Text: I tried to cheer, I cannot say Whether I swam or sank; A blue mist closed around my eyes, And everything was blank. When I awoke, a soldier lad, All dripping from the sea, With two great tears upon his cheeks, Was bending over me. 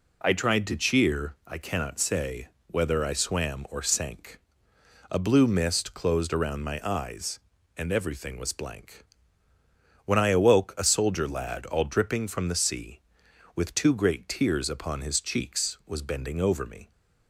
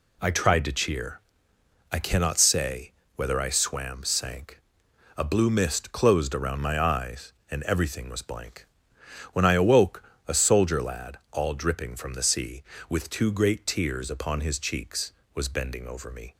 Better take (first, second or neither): first